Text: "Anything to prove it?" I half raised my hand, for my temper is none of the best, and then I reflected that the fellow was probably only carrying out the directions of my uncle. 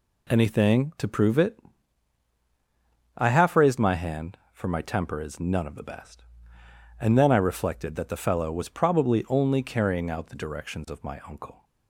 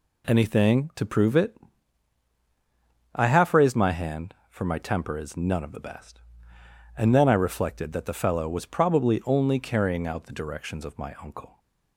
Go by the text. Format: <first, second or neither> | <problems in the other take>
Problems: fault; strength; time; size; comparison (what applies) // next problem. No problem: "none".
neither | none